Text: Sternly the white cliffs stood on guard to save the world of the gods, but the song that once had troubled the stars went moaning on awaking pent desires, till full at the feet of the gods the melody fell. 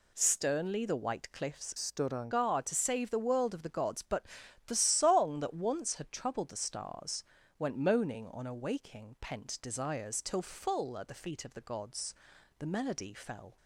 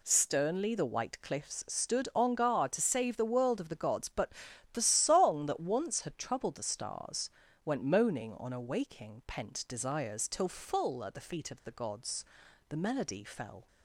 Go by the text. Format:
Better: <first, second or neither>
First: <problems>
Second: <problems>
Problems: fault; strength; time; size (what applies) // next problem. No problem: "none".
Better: second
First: changes voice from "stood" to "on"; from 1.7 to 2.2 s; 0.5 s long // pauses between "but" and "the"; at 4.2 s; 0.40 s long // pauses between "stars" and "went"; slight; at 7.2 s; 0.34 s long // pauses between "gods" and "the"; noticeable; at 12.1 s; 0.46 s long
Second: pauses between "but" and "the"; at 4.3 s; 0.40 s long // pauses between "stars" and "went"; slight; at 7.3 s; 0.34 s long // pauses between "gods" and "the"; noticeable; at 12.2 s; 0.46 s long